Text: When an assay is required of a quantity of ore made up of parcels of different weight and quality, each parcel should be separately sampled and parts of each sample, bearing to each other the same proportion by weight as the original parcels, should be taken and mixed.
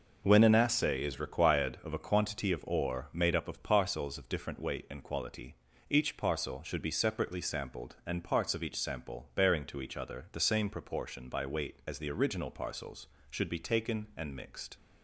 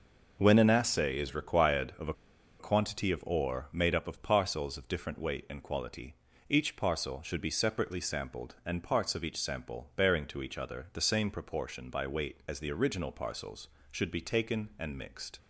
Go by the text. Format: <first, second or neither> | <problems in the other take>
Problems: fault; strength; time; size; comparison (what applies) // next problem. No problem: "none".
first | pauses between "a" and "quantity"; noticeable; at 2.1 s; 0.46 s long